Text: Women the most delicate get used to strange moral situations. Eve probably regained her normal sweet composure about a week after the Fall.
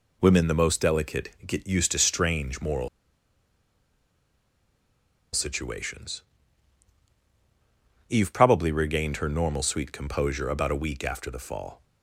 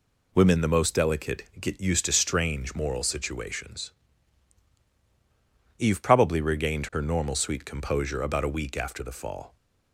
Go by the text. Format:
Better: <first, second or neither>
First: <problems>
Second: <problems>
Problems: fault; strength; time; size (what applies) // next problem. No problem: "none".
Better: second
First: pauses between "delicate" and "get"; slight; at 1.2 s; 0.18 s long // pauses between "moral" and "situations"; strong; at 2.8 s; 2.4 s long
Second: pauses between "delicate" and "get"; slight; at 1.4 s; 0.18 s long